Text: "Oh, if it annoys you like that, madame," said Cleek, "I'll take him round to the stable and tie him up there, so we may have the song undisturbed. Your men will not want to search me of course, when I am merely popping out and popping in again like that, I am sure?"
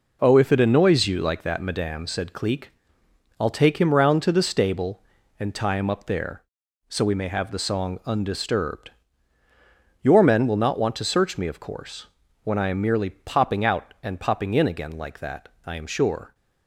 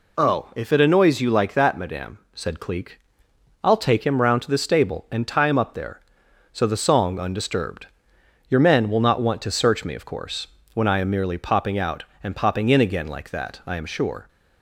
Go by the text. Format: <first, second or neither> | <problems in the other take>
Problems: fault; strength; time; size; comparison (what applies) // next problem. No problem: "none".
first | skips "we may have"; at 6.6 s